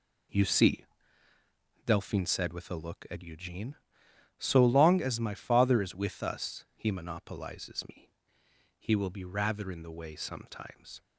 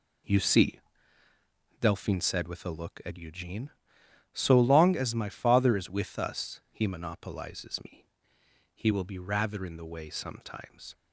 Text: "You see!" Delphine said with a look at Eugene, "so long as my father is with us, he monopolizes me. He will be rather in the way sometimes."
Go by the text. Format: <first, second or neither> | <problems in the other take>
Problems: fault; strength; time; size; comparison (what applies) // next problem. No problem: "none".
neither | none